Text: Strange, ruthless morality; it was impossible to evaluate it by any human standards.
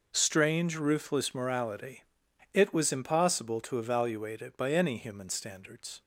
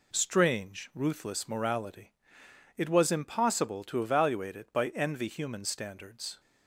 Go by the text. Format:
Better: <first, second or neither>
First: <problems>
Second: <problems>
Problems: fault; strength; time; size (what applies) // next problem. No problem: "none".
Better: first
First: none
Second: says "envy" for "any"; at 4.8 s